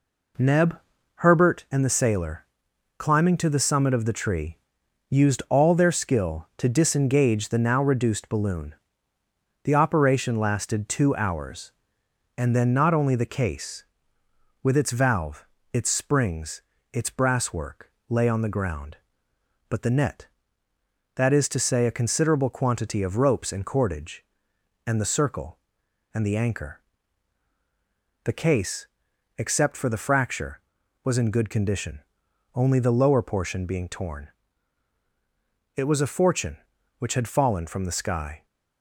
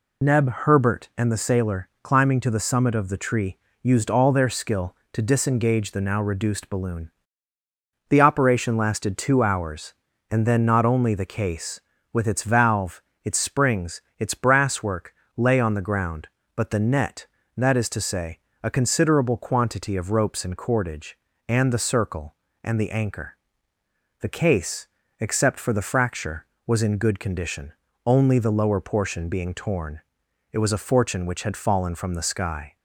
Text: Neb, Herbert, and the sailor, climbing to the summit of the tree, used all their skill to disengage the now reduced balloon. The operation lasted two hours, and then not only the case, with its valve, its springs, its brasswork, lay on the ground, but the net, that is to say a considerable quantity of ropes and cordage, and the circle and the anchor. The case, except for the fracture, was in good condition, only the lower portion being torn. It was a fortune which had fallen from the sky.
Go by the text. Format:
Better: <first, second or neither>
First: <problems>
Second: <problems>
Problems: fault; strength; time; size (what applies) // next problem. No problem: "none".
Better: first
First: none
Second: loses the start of "Neb"; at 0.2 s; 55 ms // pauses between "say" and "a"; slight; at 18.3 s; 0.24 s long